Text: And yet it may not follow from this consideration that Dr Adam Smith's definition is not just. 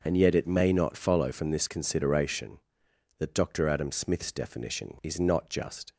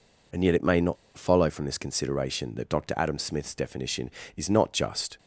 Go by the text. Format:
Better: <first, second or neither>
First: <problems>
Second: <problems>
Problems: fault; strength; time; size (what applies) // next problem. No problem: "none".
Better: first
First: none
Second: pauses between "not" and "follow"; slight; at 0.9 s; 0.21 s long